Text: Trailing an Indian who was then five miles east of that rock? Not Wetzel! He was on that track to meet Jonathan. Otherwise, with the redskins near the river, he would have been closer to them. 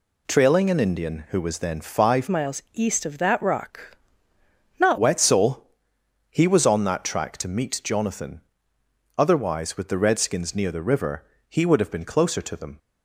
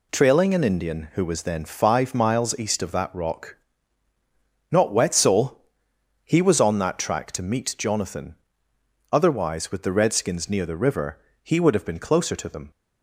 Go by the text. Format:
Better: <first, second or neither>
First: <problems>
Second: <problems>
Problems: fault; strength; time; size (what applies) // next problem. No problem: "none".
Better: second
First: changes voice from "miles" to "Not"; from 2.2 to 4.9 s; 2.7 s long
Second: none